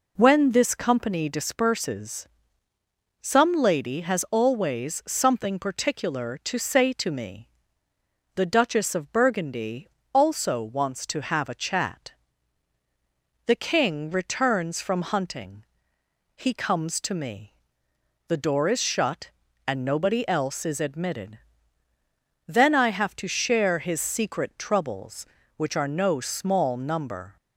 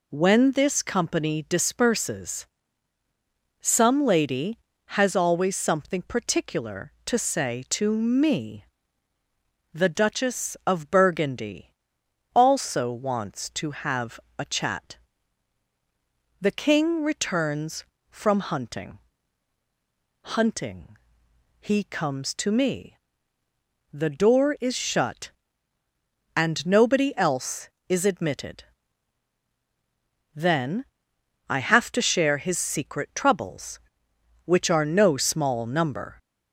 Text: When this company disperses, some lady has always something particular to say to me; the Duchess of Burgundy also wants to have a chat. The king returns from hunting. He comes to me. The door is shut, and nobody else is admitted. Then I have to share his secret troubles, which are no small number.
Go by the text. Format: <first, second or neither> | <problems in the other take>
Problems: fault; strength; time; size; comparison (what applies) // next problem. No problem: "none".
first | pauses between "Burgundy" and "also"; noticeable; at 11.7 s; 0.64 s long; slight in the first // pauses between "have" and "a"; slight; at 14.1 s; 0.18 s long // says "hunting" twice; at 20.2 s // pauses between "Then" and "I"; noticeable; at 30.8 s; 0.64 s long